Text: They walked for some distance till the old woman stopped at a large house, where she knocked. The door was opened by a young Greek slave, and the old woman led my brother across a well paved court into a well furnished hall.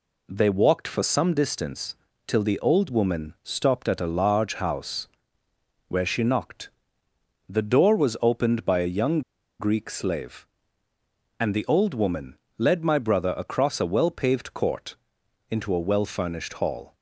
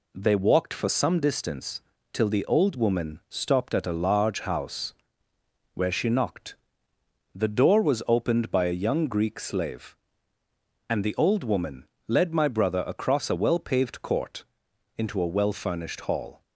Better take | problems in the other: second | pauses between "distance" and "till"; slight; at 1.9 s; 0.32 s long; slight in the second // pauses between "young" and "Greek"; at 9.2 s; 0.38 s long // pauses between "woman" and "led"; slight; at 12.3 s; 0.20 s long; slight in the second // pauses between "court" and "into"; noticeable; at 14.9 s; 0.56 s long; noticeable in the second

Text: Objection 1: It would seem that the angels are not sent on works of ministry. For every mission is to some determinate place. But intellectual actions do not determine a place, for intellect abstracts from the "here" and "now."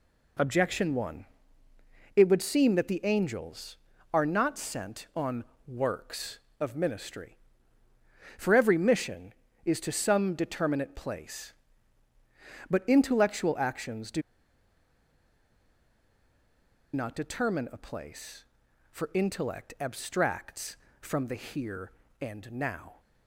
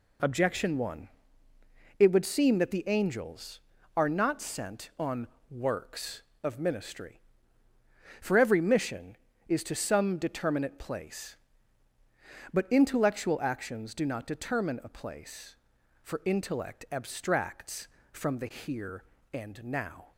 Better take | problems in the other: second | pauses between "on" and "works"; slight; at 5.4 s; 0.22 s long; slight in the second // pauses between "do" and "not"; strong; at 14.2 s; 2.7 s long

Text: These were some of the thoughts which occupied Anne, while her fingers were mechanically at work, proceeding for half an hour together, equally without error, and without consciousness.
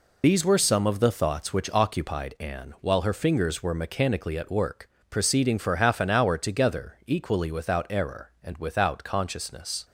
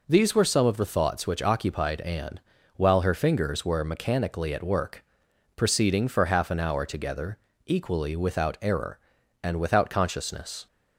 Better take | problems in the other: second | loses the start of "These"; at 0.2 s; 30 ms

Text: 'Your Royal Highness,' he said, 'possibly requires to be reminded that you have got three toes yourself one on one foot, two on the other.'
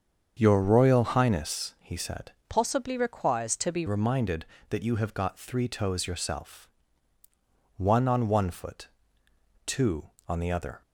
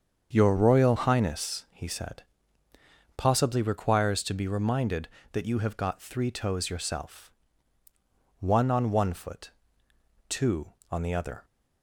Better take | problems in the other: second | starts louder than the rest; until 1.4 s; 7 dB; also in the second // changes voice from "possibly" to "be"; from 2.4 to 3.8 s; 1.4 s long // pauses between "yourself" and "one"; at 6.6 s; 1.0 s long; also in the second

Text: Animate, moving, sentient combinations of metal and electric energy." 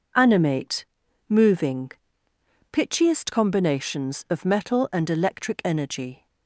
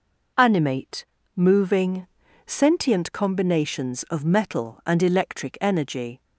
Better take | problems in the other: second | says "pitchiest" for "sentient"; at 2.7 s

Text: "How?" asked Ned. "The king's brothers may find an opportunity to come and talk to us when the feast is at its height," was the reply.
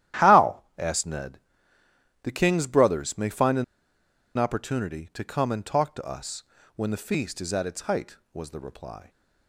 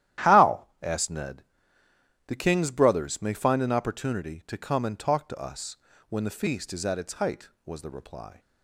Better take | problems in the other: second | starts louder than the rest; strong; until 1.3 s; 12 dB; strong in the second // pauses between "an" and "opportunity"; noticeable; at 3.6 s; 0.73 s long // pauses between "us" and "when"; slight; at 6.4 s; 0.32 s long; slight in the second

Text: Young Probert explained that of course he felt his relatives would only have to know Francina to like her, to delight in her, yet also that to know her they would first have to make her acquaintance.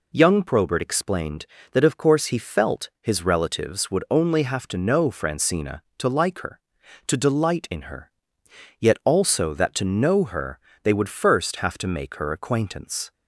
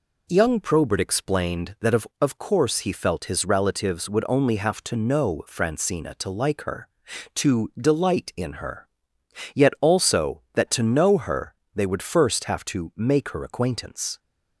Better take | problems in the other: first | says "of" twice; at 2.1 s // pauses between "her" and "they"; slight; at 11.5 s; 0.20 s long; slight in the first

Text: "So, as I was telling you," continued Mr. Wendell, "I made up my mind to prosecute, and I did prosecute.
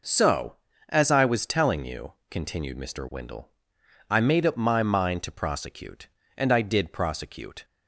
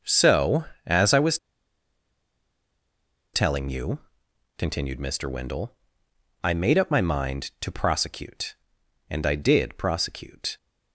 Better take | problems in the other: first | starts louder than the rest; noticeable; until 1.2 s; 6 dB // pauses between "was" and "telling"; strong; at 1.3 s; 1.9 s long

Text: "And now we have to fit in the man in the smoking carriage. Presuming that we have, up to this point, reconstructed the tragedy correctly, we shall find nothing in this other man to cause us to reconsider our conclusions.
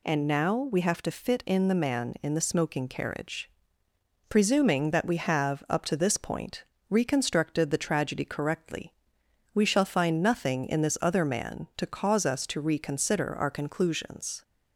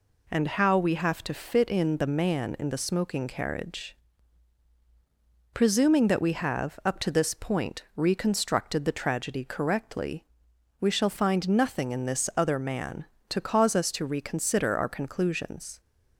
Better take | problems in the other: first | says "how" for "now"; at 0.4 s

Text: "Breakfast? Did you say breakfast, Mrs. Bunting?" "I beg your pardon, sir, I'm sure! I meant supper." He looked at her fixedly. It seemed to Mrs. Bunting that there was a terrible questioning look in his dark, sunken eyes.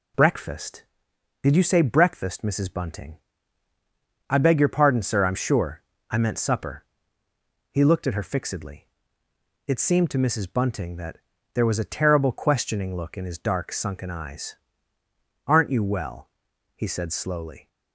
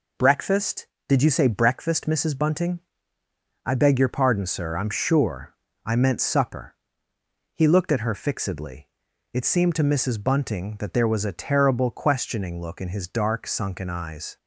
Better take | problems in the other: second | pauses between "that" and "there"; slight; at 11.1 s; 0.36 s long // goes on to say "Aren't you well he said slowly"; strong; from 15.4 s on; 2.2 s long

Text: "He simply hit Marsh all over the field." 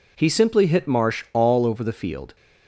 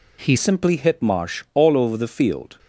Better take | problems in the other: first | changes voice at "simply"; from 0.3 s on; 2.2 s long

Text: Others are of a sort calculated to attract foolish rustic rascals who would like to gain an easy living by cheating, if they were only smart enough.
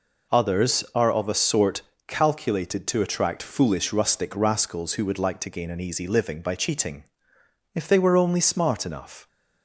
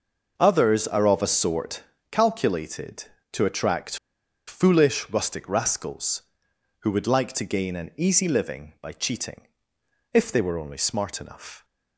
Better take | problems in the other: first | pauses between "sort" and "calculated"; slight; at 1.8 s; 0.30 s long; slight in the first // pauses between "attract" and "foolish"; noticeable; at 3.9 s; 0.51 s long

